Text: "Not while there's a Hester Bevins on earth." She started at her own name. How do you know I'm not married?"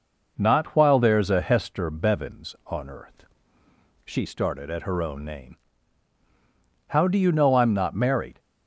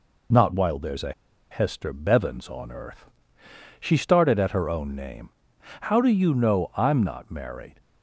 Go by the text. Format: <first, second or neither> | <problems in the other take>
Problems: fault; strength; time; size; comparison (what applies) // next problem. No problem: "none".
first | pauses between "a" and "Hester"; at 1.1 s; 0.39 s long